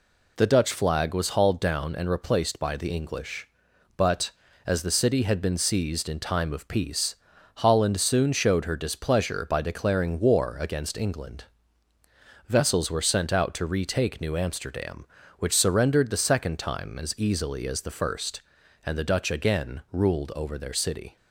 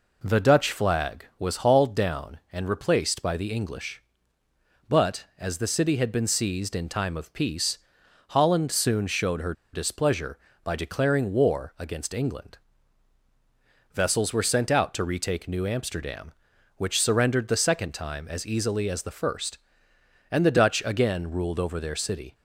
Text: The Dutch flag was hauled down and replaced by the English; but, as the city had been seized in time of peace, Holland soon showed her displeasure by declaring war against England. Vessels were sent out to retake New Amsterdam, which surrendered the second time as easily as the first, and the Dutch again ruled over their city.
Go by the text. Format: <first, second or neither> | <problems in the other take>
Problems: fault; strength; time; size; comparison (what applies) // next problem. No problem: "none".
first | pauses between "her" and "displeasure"; slight; at 9.5 s; 0.21 s long